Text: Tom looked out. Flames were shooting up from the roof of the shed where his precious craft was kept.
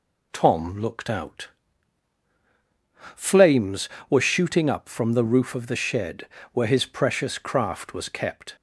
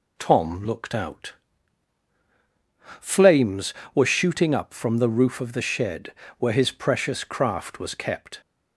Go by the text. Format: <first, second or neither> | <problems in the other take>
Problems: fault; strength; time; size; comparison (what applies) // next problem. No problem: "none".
neither | pauses between "shed" and "where"; slight; the same in both